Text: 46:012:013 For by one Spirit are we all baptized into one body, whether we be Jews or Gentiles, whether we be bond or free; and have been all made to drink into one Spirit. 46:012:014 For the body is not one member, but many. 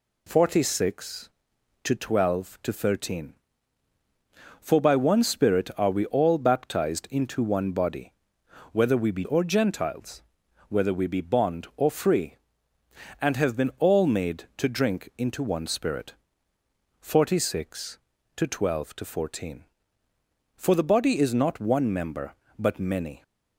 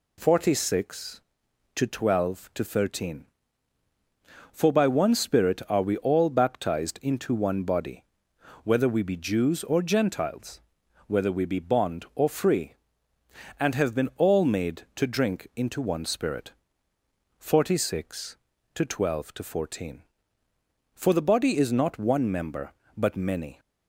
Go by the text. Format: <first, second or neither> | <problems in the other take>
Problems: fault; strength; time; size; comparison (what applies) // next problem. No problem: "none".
second | skips "Jews"; at 9.2 s